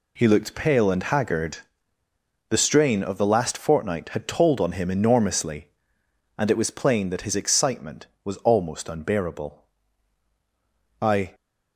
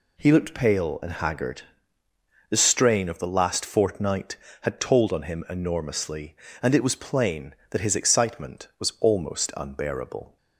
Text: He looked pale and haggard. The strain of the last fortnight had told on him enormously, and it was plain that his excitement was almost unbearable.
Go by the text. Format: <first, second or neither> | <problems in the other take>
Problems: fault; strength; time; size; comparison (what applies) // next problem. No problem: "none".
second | goes on to say "I"; slight; from 11.0 s on; 0.32 s long